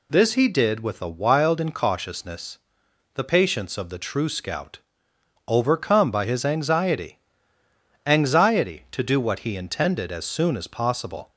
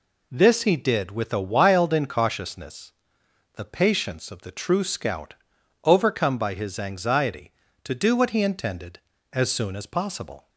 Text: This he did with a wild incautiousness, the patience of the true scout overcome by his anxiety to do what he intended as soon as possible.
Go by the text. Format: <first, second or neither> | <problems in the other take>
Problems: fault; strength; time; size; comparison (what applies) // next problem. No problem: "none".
second | pauses between "scout" and "overcome"; noticeable; at 4.7 s; 0.68 s long; noticeable in the second // says "anxiety" twice; at 8.0 s